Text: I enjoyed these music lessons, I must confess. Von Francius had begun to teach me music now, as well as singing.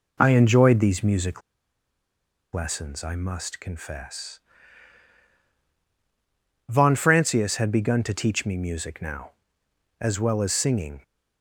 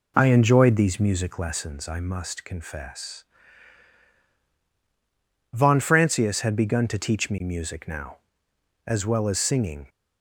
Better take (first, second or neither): second